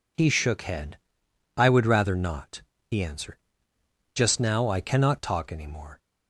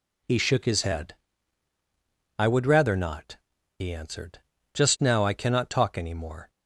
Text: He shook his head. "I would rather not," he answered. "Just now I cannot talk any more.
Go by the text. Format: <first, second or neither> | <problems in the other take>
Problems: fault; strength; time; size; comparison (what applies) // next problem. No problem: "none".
second | skips "his"; at 0.6 s